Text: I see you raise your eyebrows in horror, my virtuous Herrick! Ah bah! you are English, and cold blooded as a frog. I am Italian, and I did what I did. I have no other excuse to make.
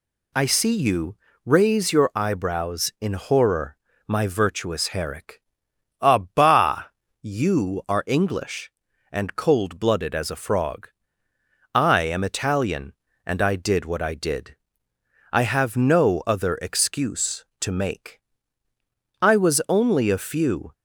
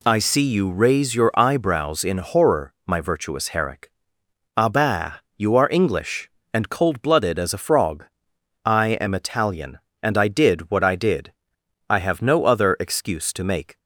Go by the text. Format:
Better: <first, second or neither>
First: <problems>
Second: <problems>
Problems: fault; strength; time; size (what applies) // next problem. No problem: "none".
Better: second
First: pauses between "you" and "raise"; slight; at 1.1 s; 0.28 s long // goes on to say "I was only a few"; from 19.2 s on; 1.5 s long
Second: none